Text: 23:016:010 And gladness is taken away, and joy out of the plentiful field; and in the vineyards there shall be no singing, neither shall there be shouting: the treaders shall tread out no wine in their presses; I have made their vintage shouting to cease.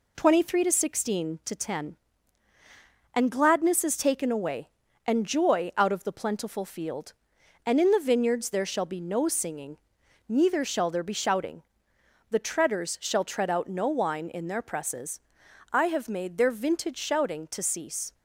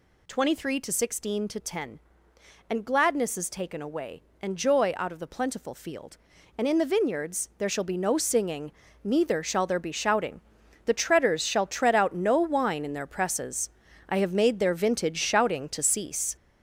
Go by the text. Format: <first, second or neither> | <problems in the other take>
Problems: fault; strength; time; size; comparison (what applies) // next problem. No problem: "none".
first | gets louder; throughout; 6.5 dB